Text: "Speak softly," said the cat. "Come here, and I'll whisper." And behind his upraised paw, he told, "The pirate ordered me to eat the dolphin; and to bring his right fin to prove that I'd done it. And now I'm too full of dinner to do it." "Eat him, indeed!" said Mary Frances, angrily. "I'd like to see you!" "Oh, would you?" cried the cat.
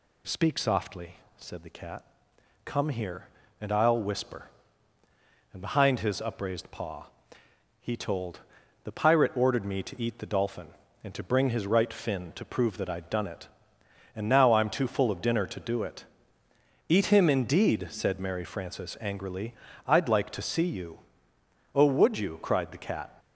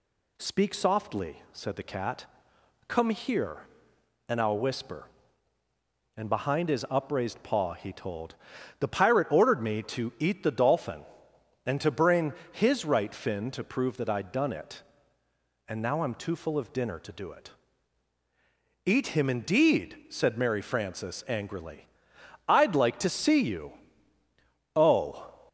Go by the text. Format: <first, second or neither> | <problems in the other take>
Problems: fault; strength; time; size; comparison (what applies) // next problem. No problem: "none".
first | pauses between "bring" and "his"; slight; at 12.3 s; 0.20 s long // stops before "would you cried the cat"; at 25.4 s